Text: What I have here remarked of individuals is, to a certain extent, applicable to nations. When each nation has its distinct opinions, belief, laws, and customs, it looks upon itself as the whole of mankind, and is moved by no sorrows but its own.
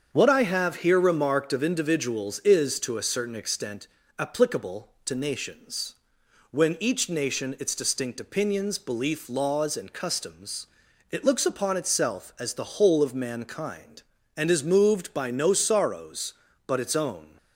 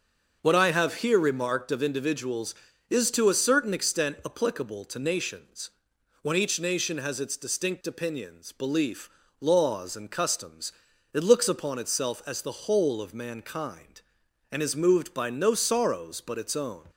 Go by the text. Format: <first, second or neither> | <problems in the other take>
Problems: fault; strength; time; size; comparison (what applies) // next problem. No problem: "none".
second | starts louder than the rest; strong; until 1.1 s; 7 dB; noticeable in the second // skips "has"; at 7.5 s